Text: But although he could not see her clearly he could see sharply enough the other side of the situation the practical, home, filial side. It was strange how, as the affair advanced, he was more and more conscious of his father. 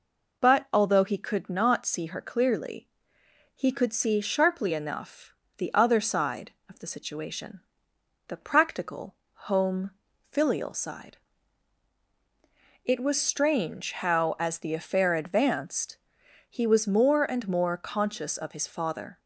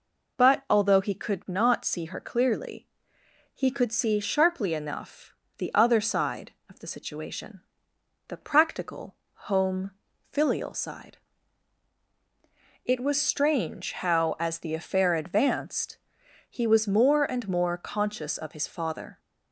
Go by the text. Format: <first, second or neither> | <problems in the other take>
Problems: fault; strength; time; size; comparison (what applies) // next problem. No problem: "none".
neither | pauses between "clearly" and "he"; noticeable; the same in both // pauses between "enough" and "the"; slight; the same in both // pauses between "situation" and "the"; noticeable; the same in both